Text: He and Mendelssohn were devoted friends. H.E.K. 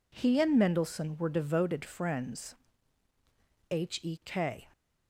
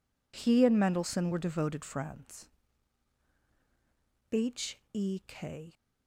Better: neither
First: none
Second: none

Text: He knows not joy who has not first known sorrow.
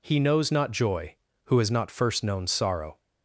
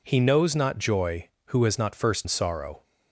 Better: first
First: none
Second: skips "known"; at 2.2 s

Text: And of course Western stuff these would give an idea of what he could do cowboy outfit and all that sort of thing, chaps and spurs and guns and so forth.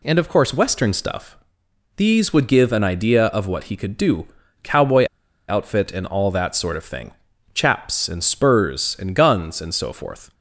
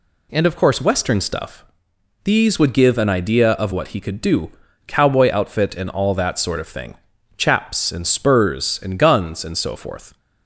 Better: second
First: pauses between "stuff" and "these"; noticeable; at 1.3 s; 0.60 s long // pauses between "do" and "cowboy"; slight; at 4.2 s; 0.36 s long // pauses between "cowboy" and "outfit"; at 5.0 s; 0.43 s long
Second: pauses between "stuff" and "these"; noticeable; at 1.6 s; 0.60 s long // pauses between "do" and "cowboy"; slight; at 4.5 s; 0.36 s long

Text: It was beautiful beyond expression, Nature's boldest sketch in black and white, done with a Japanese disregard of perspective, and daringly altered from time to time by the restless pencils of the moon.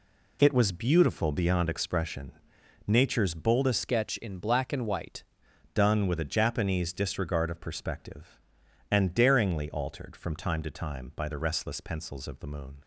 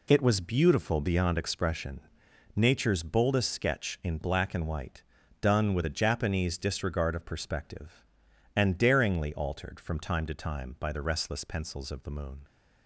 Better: second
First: changes voice from "sketch" to "white"; from 3.8 to 5.2 s; 1.4 s long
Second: none

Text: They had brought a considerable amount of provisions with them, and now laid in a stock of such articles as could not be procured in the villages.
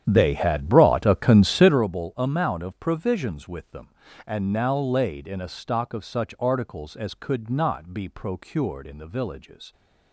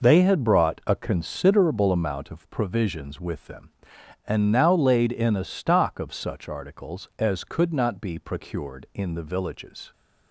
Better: second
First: starts louder than the rest; strong; until 1.9 s; 9.5 dB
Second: none

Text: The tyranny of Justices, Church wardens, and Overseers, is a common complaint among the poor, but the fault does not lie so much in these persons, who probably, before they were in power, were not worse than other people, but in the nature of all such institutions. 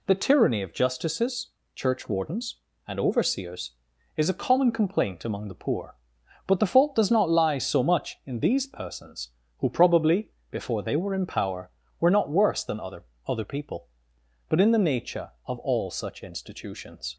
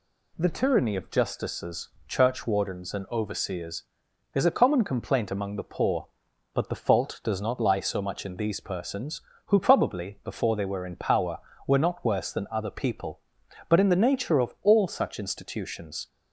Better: second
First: says "other" twice; at 13.2 s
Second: none

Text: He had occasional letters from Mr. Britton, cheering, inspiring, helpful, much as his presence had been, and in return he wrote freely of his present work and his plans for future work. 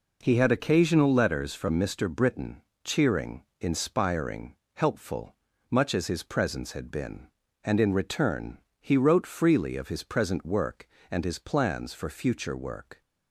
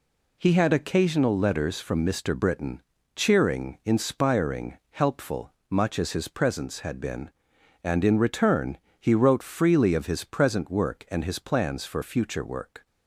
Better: neither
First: pauses between "return" and "he"; slight; at 8.5 s; 0.20 s long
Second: pauses between "return" and "he"; slight; at 8.7 s; 0.22 s long

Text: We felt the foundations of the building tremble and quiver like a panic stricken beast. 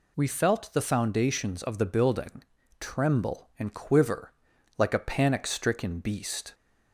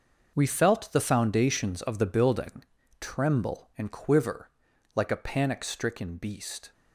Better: first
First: pauses between "building" and "tremble"; slight; at 2.4 s; 0.36 s long // pauses between "quiver" and "like"; noticeable; at 4.3 s; 0.46 s long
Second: gets quieter; strong; throughout; 10.5 dB // pauses between "building" and "tremble"; slight; at 2.6 s; 0.36 s long // pauses between "quiver" and "like"; noticeable; at 4.4 s; 0.46 s long

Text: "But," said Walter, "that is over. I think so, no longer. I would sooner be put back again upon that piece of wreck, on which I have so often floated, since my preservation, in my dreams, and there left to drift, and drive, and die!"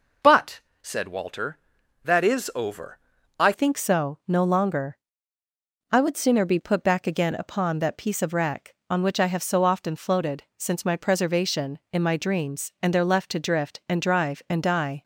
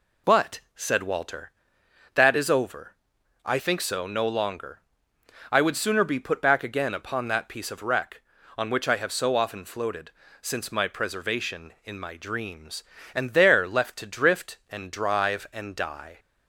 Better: second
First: changes voice at "think"; from 3.5 s on; 11.5 s long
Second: none

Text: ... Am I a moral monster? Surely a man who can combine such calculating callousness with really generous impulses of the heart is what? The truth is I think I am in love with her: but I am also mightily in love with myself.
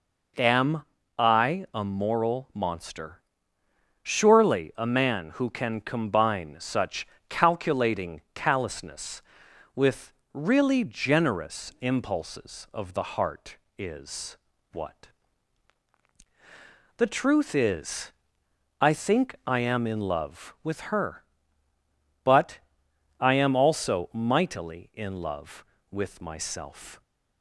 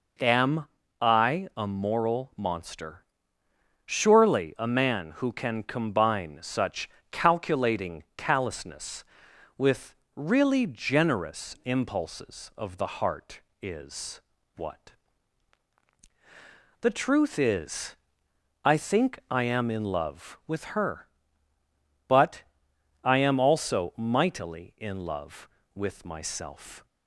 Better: neither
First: pauses between "Am" and "I"; slight; at 0.8 s; 0.34 s long // pauses between "such" and "calculating"; slight; at 7.0 s; 0.24 s long // pauses between "with" and "really"; slight; at 10.1 s; 0.22 s long // pauses between "is" and "what"; slight; at 14.3 s; 0.34 s long // pauses between "is" and "I"; noticeable; at 18.1 s; 0.68 s long // pauses between "but" and "I"; noticeable; at 22.5 s; 0.60 s long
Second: pauses between "Am" and "I"; slight; at 0.6 s; 0.34 s long // pauses between "such" and "calculating"; slight; at 6.8 s; 0.24 s long // pauses between "with" and "really"; slight; at 9.9 s; 0.22 s long // pauses between "is" and "what"; slight; at 14.2 s; 0.34 s long // pauses between "is" and "I"; noticeable; at 17.9 s; 0.68 s long // pauses between "but" and "I"; noticeable; at 22.4 s; 0.60 s long

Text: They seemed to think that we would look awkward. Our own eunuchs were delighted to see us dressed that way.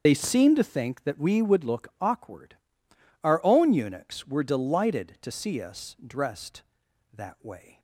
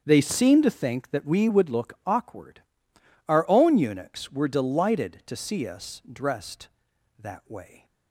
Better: second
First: loses the start of "They"; at 0.0 s; 65 ms // starts louder than the rest; until 1.0 s; 7 dB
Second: starts louder than the rest; strong; until 1.0 s; 7.5 dB

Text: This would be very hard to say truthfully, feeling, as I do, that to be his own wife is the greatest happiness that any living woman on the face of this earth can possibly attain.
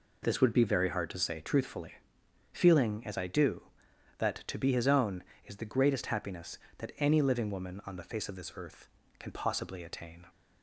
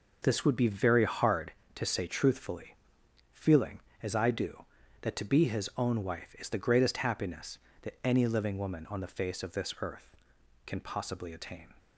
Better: second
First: skips "wife"; at 5.3 s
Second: none

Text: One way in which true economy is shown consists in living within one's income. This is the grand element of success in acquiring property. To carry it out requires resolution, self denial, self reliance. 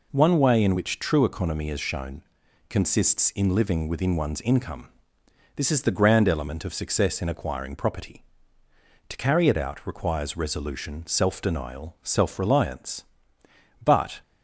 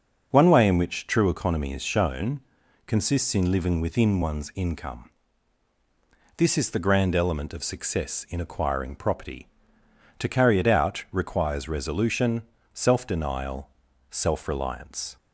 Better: second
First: pauses between "shown" and "consists"; noticeable; at 2.2 s; 0.48 s long // goes on to say "But"; slight; from 13.8 s on; 0.38 s long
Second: pauses between "shown" and "consists"; noticeable; at 2.3 s; 0.46 s long

